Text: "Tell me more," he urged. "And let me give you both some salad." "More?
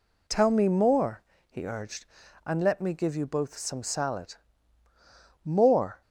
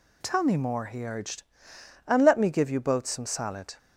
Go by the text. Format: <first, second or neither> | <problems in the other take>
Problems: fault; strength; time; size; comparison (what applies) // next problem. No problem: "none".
first | stops before "More"; at 3.7 s